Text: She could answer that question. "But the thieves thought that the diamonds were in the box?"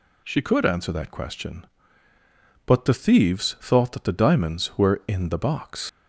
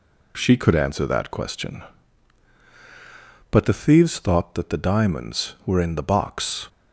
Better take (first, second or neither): second